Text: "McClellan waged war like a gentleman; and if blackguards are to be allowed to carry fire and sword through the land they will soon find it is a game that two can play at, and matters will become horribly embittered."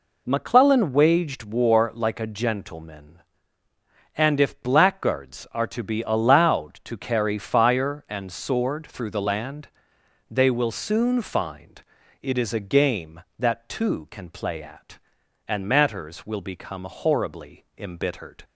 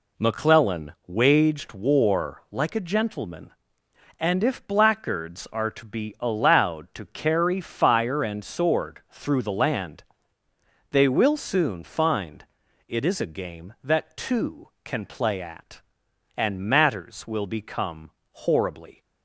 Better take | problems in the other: first | pauses between "land" and "they"; noticeable; at 10.0 s; 0.86 s long; noticeable in the first // pauses between "find" and "it"; at 12.4 s; 0.42 s long; also in the first // pauses between "become" and "horribly"; slight; at 18.1 s; 0.20 s long // stops before "embittered"; at 19.0 s

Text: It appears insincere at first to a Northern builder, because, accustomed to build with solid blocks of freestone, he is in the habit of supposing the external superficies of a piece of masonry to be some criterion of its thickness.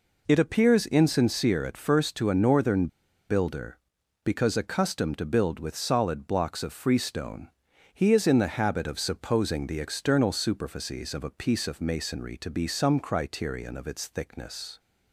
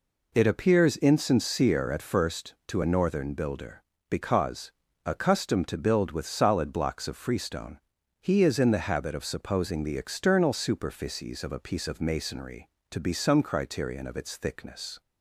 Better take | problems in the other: second | pauses between "Northern" and "builder"; at 2.8 s; 0.42 s long

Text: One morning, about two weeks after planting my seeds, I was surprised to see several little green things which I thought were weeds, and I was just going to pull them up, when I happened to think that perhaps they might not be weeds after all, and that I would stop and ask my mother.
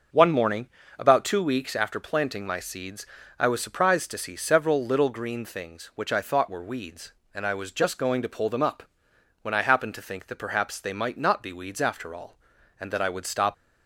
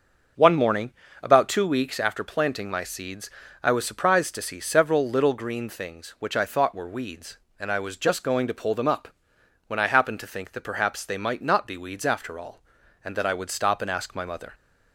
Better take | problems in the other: second | starts louder than the rest; until 1.4 s; 6 dB; also in the second // stops before "and ask my mother"; at 13.5 s

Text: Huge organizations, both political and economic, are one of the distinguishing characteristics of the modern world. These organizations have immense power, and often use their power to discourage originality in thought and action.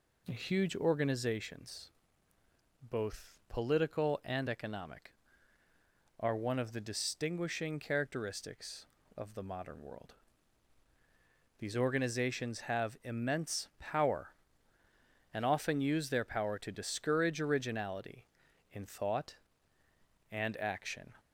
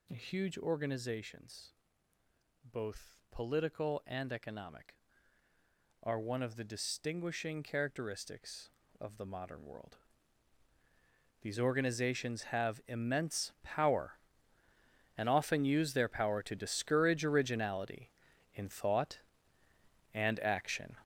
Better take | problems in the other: first | gets louder; strong; throughout; 9.5 dB

